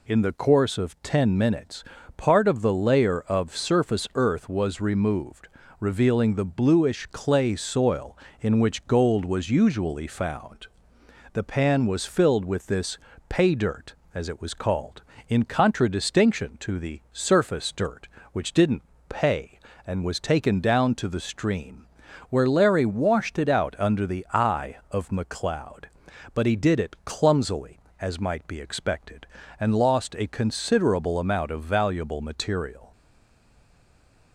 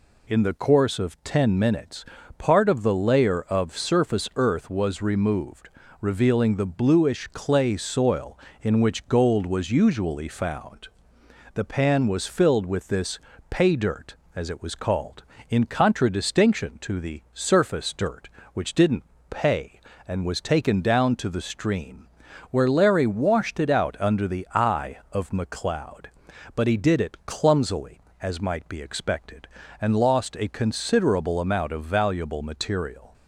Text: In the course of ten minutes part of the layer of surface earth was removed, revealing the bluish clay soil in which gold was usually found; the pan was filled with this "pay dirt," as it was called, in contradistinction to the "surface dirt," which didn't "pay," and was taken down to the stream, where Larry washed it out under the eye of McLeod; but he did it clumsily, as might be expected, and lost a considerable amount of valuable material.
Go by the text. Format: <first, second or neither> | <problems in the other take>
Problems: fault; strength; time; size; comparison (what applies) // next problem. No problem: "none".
second | pauses between "minutes" and "part"; slight; at 1.8 s; 0.34 s long; slight in the second // pauses between "this" and "pay"; slight; at 12.9 s; 0.30 s long; slight in the second // pauses between "didn't" and "pay"; slight; at 18.8 s; 0.26 s long; slight in the second // stays silent after the last word; noticeable; from 32.9 s on; 1.4 s long